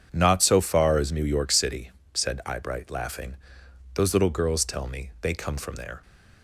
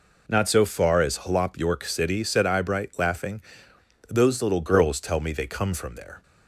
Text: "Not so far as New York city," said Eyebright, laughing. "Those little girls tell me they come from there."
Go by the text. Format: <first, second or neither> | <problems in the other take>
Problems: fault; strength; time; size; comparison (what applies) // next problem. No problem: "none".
first | says "Hlop" for "New"; at 1.2 s